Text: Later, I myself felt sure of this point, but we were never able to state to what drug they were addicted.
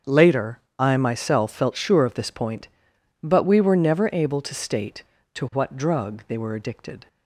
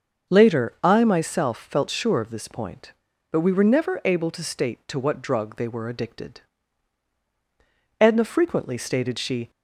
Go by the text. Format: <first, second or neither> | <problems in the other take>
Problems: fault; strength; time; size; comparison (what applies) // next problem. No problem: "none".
first | starts louder than the rest; until 1.4 s; 6.5 dB; also in the first // goes on to say "Edna frequently stated she"; from 7.9 s on; 1.5 s long